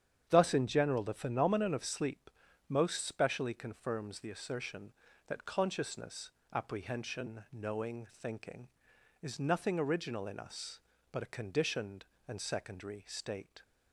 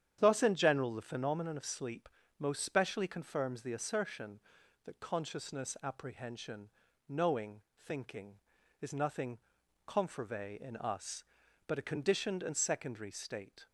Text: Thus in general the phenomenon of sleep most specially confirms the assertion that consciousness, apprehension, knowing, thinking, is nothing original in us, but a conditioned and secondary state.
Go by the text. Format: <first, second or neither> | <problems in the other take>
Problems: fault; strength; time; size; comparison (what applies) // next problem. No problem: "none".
first | starts louder than the rest; strong; until 1.2 s; 9.5 dB; strong in the first // pauses between "sleep" and "most"; slight; at 2.0 s; 0.30 s long; also in the first // says "confervae" for "original"; at 9.8 s